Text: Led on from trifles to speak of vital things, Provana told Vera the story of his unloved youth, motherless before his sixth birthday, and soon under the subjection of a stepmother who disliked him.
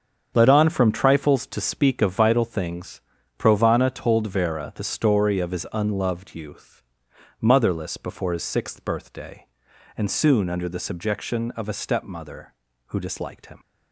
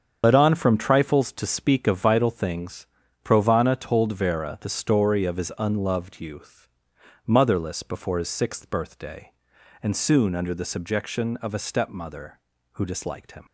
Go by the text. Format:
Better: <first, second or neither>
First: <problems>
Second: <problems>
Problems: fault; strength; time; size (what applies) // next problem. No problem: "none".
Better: first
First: starts louder than the rest; strong; until 1.3 s; 7.5 dB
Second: loses the start of "Led"; at 0.2 s; 35 ms // starts louder than the rest; strong; until 1.2 s; 7.5 dB